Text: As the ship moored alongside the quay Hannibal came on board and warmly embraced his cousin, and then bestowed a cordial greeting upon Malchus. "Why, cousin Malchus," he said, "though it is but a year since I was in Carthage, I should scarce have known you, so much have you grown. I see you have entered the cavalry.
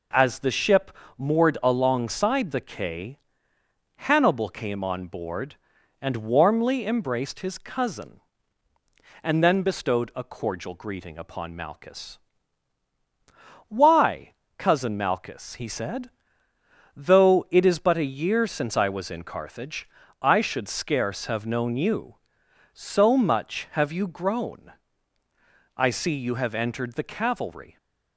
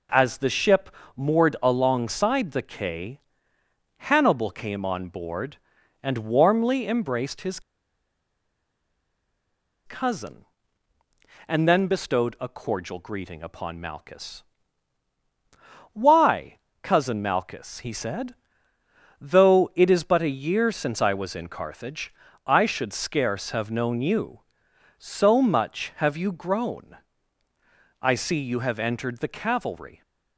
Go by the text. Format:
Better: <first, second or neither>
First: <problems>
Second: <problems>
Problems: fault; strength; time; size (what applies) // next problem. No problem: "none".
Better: first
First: pauses between "ship" and "moored"; slight; at 0.9 s; 0.26 s long // pauses between "quay" and "Hannibal"; noticeable; at 3.1 s; 0.78 s long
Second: pauses between "ship" and "moored"; slight; at 0.9 s; 0.26 s long // pauses between "quay" and "Hannibal"; noticeable; at 3.2 s; 0.78 s long // pauses between "his" and "cousin"; strong; at 7.6 s; 2.2 s long